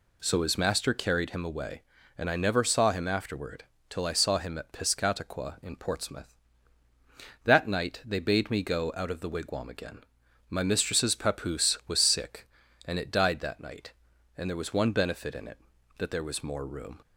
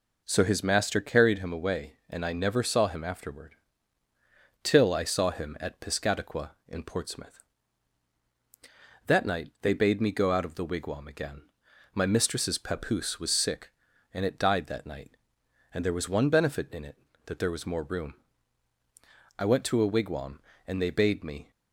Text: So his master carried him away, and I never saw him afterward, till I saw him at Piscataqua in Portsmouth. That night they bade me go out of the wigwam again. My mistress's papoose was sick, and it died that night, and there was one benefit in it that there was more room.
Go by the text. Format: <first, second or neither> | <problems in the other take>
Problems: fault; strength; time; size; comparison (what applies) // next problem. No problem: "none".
first | goes on to say "I went to a wigwam and they bade me"; strong; from 19.3 s on; 2.1 s long